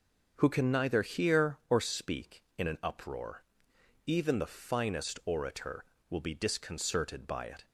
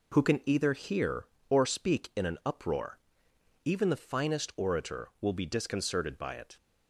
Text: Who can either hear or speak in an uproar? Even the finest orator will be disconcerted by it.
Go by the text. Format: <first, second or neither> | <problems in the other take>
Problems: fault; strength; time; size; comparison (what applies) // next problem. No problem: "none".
second | says "neither" for "either"; at 0.7 s